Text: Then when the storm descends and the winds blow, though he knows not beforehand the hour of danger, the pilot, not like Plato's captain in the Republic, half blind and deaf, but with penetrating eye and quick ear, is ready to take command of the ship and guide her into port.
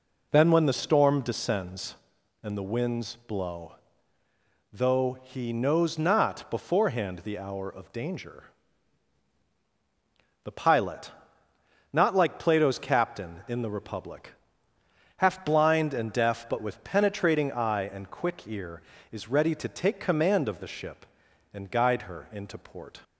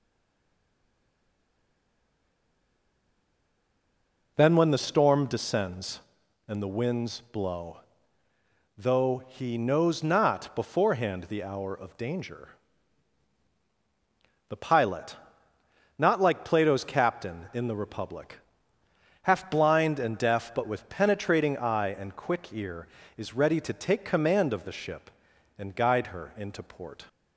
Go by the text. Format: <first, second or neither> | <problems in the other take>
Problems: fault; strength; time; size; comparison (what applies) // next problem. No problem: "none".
first | stays silent before the first word; strong; until 4.3 s; 4.3 s long